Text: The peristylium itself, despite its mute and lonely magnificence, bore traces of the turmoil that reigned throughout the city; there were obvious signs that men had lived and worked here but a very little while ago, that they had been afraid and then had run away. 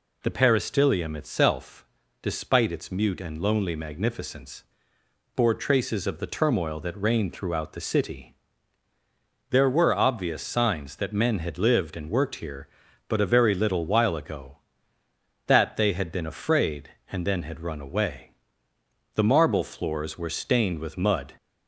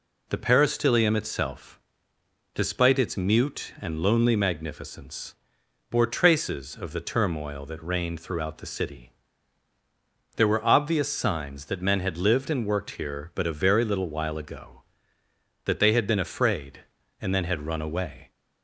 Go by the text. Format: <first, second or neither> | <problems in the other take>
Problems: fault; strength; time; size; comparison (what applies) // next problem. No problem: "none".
second | goes on to say "The marble floors were stained with mud"; strong; from 19.1 s on; 2.2 s long